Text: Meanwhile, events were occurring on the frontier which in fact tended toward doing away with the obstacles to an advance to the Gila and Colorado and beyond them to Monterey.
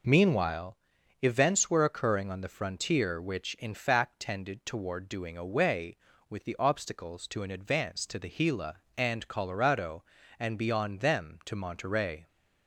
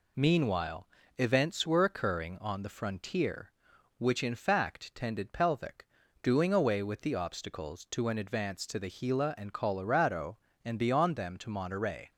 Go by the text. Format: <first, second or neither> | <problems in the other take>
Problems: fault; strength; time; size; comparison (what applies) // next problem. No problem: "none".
first | says "pelvic" for "toward"; at 5.3 s